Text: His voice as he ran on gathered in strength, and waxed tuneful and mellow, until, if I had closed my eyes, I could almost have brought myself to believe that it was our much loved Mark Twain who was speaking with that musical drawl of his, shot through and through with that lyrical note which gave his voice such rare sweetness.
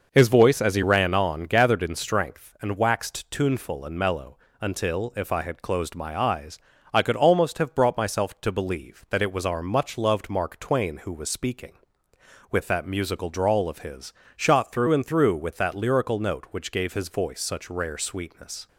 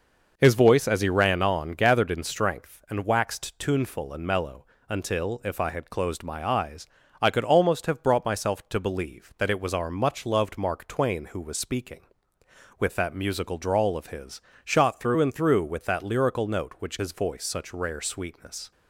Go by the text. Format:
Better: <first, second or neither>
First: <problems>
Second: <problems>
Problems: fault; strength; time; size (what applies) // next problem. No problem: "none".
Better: first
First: none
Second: skips "gave"; at 16.9 s